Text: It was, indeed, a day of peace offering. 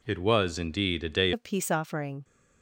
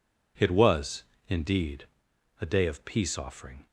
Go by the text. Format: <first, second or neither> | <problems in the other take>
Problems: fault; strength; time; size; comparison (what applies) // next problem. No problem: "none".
second | changes voice at "of"; from 1.3 s on; 0.9 s long